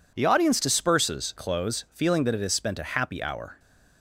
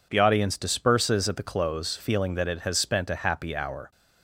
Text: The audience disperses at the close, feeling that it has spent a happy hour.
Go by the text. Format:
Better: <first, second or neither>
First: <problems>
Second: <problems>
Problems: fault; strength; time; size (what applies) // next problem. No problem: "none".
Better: second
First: skips "at the"; at 1.3 s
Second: none